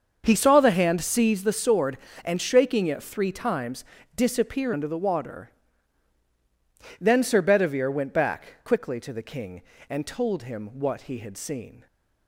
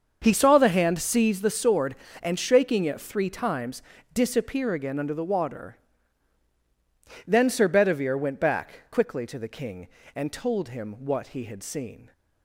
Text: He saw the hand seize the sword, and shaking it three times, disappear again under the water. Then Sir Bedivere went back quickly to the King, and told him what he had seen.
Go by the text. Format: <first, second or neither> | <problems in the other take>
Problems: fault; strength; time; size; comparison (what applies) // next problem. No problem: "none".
second | starts louder than the rest; until 1.2 s; 6.5 dB; also in the second // skips "again"; at 4.7 s